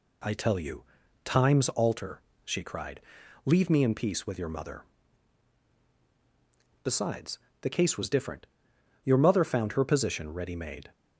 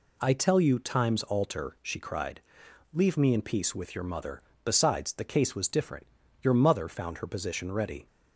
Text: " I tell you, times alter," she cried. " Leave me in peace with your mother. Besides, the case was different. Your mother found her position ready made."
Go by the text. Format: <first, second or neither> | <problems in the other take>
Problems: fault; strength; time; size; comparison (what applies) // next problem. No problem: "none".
first | stops before "made"; at 8.0 s